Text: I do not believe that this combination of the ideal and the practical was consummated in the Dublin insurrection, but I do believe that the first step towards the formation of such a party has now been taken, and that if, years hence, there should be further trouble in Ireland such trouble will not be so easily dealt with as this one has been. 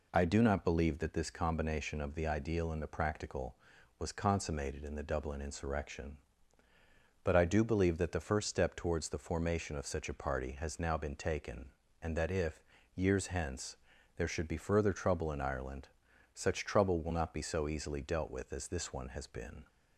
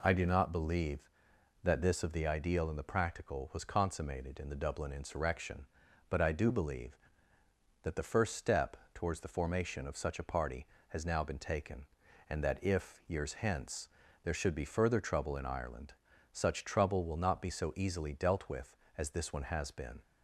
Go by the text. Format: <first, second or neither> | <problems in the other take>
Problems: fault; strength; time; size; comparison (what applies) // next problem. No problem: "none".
first | skips "combination"; at 2.0 s // pauses between "step" and "towards"; slight; at 8.7 s; 0.18 s long // pauses between "Ireland" and "such"; at 15.9 s; 0.40 s long; also in the first